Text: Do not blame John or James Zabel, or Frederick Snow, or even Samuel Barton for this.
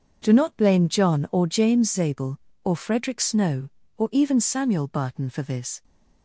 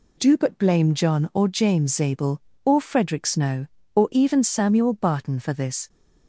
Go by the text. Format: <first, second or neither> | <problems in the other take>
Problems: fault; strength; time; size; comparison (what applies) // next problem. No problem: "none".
first | says "but" for "not"; at 0.3 s